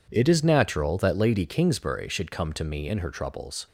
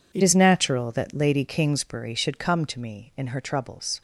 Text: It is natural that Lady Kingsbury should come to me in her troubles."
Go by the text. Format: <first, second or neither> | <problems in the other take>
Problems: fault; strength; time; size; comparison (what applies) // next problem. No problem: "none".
first | changes voice at "is"; from 0.2 s on; 3.8 s long